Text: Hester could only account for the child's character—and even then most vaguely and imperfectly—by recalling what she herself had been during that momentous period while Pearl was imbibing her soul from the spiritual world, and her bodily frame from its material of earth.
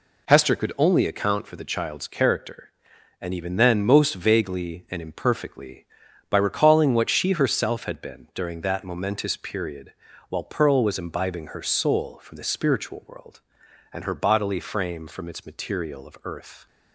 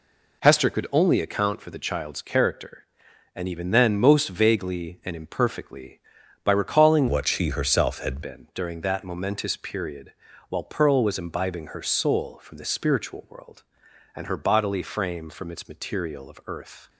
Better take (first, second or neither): first